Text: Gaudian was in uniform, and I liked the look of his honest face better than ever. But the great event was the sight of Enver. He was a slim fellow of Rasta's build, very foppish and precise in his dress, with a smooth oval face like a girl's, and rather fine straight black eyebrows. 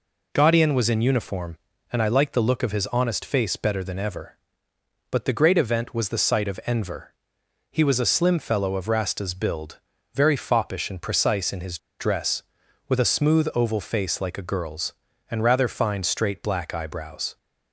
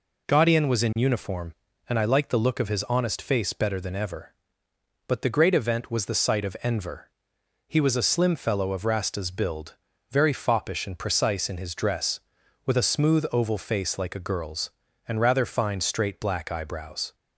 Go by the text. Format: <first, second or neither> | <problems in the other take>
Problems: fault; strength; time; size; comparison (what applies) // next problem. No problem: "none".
second | pauses between "his" and "dress"; slight; at 11.7 s; 0.21 s long